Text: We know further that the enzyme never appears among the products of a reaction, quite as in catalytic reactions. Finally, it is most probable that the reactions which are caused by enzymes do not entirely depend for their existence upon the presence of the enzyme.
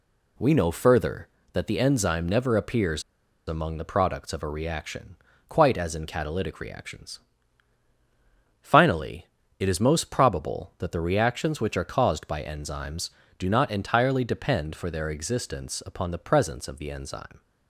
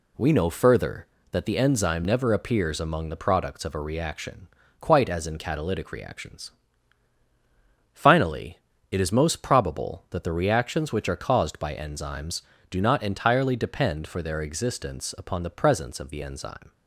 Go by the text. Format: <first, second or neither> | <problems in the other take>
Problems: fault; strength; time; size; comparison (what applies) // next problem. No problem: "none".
second | pauses between "appears" and "among"; at 3.0 s; 0.45 s long